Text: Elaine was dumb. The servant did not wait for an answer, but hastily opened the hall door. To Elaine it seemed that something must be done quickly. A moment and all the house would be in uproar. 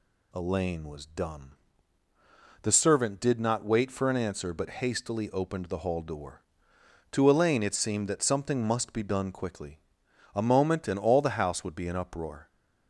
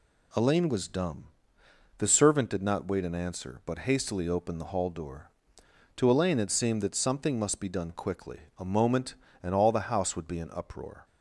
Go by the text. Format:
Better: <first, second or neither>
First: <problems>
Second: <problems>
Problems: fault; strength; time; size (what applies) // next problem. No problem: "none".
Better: first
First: none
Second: skips "for"; at 3.0 s